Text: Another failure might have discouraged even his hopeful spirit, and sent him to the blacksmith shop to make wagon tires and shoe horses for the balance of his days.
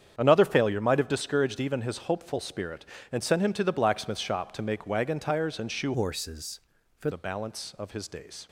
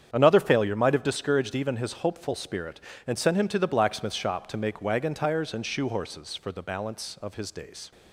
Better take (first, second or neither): second